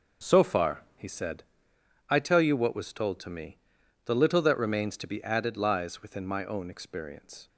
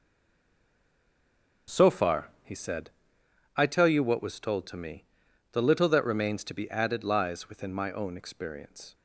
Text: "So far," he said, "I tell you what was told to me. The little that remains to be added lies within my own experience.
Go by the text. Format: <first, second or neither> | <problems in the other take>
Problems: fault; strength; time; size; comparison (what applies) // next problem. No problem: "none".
first | stays silent before the first word; noticeable; until 1.6 s; 1.6 s long // starts louder than the rest; until 2.8 s; 6 dB; noticeable in the first